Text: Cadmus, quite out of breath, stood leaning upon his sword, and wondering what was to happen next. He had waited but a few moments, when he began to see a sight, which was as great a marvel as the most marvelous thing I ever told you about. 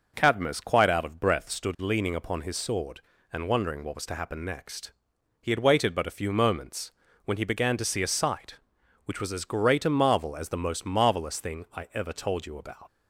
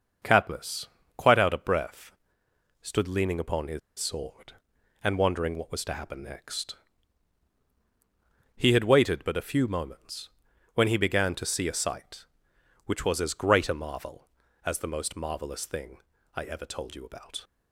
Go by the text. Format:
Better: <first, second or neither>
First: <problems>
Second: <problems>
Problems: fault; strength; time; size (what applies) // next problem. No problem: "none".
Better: first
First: none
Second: starts louder than the rest; until 1.5 s; 6.5 dB // pauses between "his" and "sword"; slight; at 3.7 s; 0.19 s long // pauses between "thing" and "I"; at 15.9 s; 0.38 s long